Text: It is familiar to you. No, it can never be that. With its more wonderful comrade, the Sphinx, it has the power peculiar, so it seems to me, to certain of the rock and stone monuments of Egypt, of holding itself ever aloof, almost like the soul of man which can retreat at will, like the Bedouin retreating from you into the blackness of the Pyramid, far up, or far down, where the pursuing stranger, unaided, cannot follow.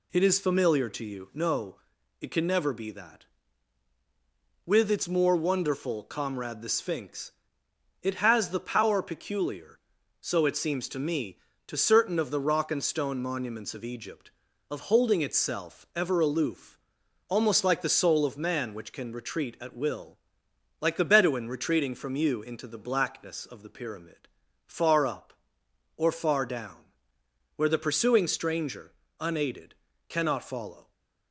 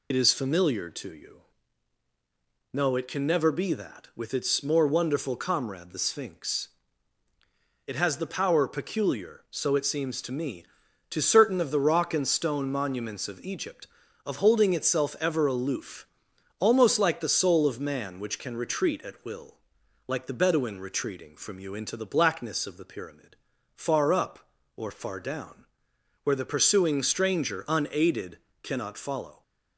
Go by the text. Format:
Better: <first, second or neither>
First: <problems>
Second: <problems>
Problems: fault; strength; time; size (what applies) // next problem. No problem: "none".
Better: first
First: none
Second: loses the start of "It"; at 0.1 s; 40 ms